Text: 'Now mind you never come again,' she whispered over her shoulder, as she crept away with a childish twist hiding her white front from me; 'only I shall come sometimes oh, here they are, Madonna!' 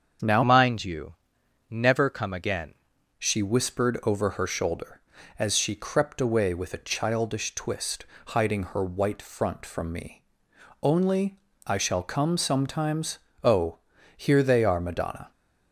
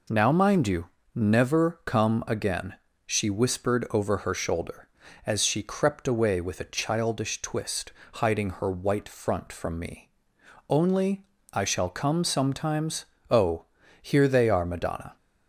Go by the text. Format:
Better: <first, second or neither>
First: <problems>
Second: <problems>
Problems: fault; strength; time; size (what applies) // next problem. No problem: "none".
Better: second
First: starts louder than the rest; until 1.7 s; 7 dB // changes voice from "mind" to "again"; from 0.4 to 2.7 s; 2.3 s long // pauses between "you" and "never"; noticeable; at 1.1 s; 0.56 s long // pauses between "twist" and "hiding"; slight; at 8.0 s; 0.22 s long // pauses between "only" and "I"; slight; at 11.3 s; 0.26 s long // pauses between "sometimes" and "oh"; slight; at 13.1 s; 0.26 s long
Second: pauses between "you" and "never"; slight; at 0.8 s; 0.26 s long // pauses between "twist" and "hiding"; slight; at 7.9 s; 0.22 s long // pauses between "only" and "I"; slight; at 11.2 s; 0.26 s long // pauses between "sometimes" and "oh"; slight; at 13.0 s; 0.26 s long